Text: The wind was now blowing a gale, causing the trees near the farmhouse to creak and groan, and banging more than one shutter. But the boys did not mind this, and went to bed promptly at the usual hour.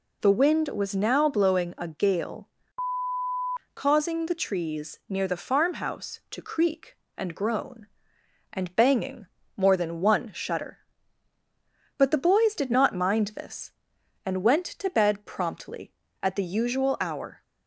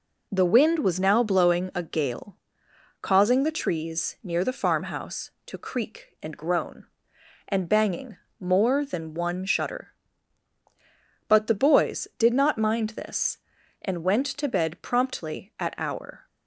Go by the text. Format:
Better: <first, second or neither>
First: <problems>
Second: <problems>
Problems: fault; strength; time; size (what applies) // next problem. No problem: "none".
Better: first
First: pauses between "banging" and "more"; slight; at 9.2 s; 0.32 s long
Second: pauses between "banging" and "more"; slight; at 8.1 s; 0.24 s long // skips "the usual"; at 15.7 s